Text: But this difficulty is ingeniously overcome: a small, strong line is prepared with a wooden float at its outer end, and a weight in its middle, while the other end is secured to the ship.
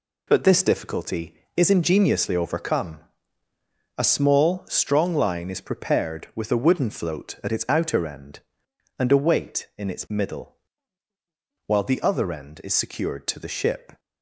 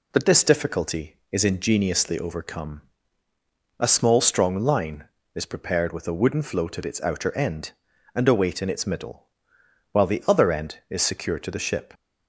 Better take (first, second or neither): neither